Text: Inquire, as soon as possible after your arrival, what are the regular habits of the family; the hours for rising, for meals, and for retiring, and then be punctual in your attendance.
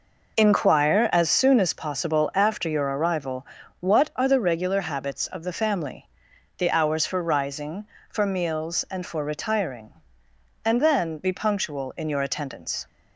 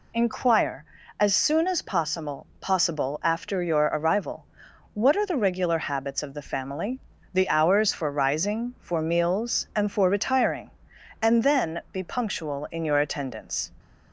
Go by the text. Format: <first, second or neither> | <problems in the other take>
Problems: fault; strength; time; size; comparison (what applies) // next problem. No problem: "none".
first | says "possible" twice; at 2.6 s